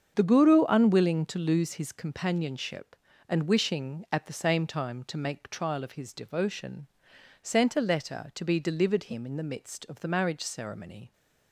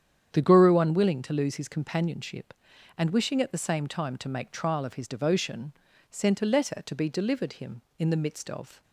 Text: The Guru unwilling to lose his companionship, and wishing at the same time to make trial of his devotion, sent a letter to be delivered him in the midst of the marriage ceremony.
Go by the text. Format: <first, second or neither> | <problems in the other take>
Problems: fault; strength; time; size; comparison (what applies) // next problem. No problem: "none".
first | starts louder than the rest; strong; until 1.3 s; 8.5 dB; also in the first // stops before "the marriage ceremony"; at 8.8 s